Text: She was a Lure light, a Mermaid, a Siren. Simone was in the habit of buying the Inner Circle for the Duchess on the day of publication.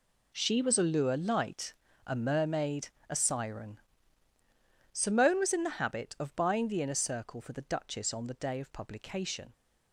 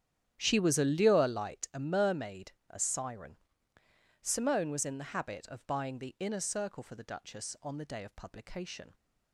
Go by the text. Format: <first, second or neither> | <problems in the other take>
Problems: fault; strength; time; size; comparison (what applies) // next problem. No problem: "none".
first | starts louder than the rest; strong; until 1.7 s; 10 dB